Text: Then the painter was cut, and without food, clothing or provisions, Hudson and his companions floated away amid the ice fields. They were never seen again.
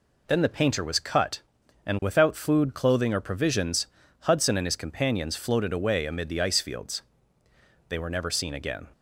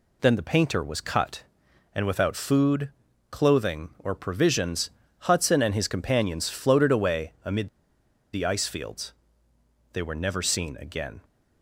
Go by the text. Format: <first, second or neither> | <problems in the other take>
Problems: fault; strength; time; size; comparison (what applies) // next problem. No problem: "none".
first | pauses between "amid" and "the"; noticeable; at 7.6 s; 0.65 s long